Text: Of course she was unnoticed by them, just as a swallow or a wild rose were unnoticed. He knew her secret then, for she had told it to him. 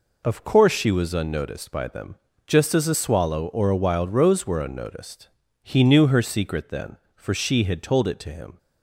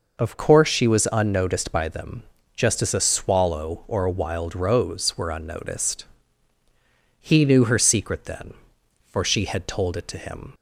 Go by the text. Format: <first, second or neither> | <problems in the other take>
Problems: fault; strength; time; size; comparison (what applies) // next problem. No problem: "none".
first | changes voice at "course"; from 0.3 s on; 10.2 s long